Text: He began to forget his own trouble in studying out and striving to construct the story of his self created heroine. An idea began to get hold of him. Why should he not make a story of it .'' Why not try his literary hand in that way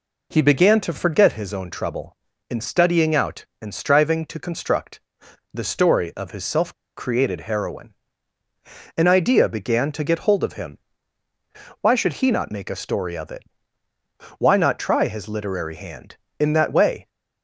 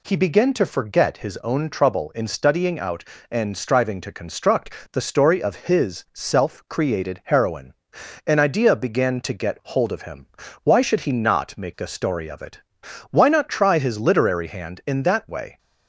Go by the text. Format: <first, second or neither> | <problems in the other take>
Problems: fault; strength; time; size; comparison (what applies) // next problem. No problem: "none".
second | pauses between "construct" and "the"; noticeable; at 5.0 s; 0.52 s long; slight in the second // pauses between "self" and "created"; slight; at 6.7 s; 0.24 s long